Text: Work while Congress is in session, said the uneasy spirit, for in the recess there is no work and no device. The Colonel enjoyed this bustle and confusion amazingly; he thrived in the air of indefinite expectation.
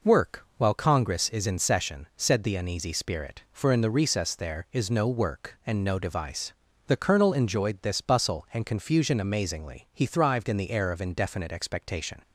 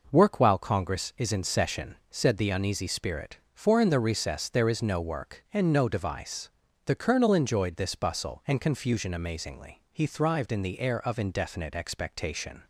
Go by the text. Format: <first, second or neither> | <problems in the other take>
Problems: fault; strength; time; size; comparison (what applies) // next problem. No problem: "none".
neither | none